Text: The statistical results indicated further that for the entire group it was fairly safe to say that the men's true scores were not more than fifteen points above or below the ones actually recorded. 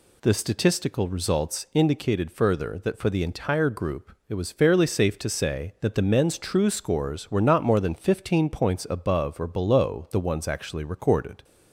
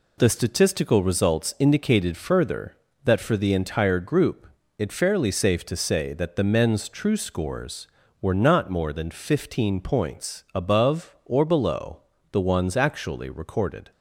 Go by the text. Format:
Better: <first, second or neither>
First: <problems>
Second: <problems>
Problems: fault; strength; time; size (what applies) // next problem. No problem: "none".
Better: first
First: pauses between "group" and "it"; slight; at 4.1 s; 0.16 s long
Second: pauses between "group" and "it"; slight; at 4.4 s; 0.30 s long // skips "was"; at 4.9 s // pauses between "below" and "the"; slight; at 12.0 s; 0.32 s long